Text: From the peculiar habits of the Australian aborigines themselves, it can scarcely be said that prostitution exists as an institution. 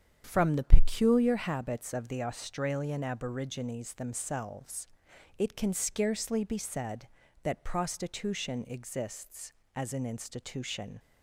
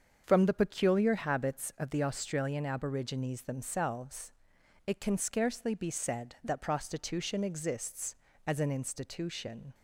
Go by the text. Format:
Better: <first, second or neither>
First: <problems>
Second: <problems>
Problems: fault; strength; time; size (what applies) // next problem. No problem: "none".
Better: neither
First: starts louder than the rest; until 1.2 s; 6 dB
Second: starts louder than the rest; until 1.2 s; 7 dB